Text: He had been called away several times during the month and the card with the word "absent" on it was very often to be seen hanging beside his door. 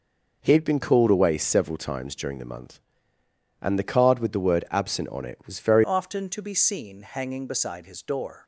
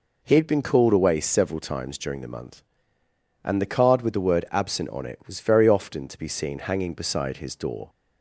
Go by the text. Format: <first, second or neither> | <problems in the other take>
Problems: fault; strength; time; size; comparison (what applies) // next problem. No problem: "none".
second | changes voice at "often"; from 5.8 s on; 2.6 s long